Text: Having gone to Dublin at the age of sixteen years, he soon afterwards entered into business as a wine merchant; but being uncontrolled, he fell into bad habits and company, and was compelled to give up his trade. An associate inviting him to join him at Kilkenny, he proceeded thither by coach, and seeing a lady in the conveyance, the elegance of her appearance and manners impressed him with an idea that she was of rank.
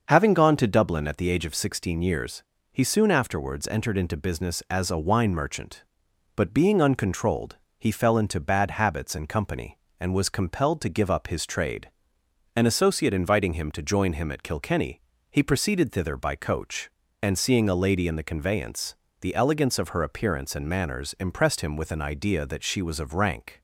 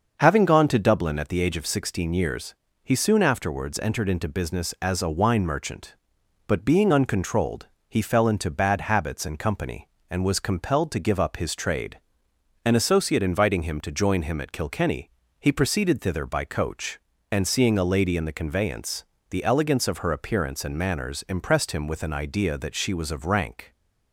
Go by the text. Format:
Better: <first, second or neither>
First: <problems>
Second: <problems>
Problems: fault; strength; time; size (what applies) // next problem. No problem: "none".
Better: neither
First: starts louder than the rest; until 1.0 s; 6.5 dB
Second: starts louder than the rest; until 1.2 s; 6.5 dB